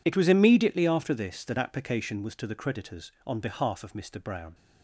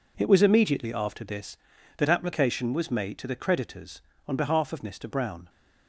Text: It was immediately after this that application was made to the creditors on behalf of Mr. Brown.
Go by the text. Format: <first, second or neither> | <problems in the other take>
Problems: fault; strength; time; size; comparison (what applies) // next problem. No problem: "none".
second | skips "made"; at 2.3 s